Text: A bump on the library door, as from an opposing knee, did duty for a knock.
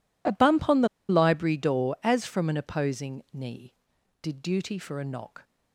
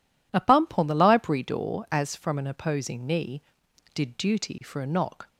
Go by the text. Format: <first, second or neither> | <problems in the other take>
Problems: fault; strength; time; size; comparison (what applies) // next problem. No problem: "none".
second | pauses between "the" and "library"; slight; at 0.8 s; 0.21 s long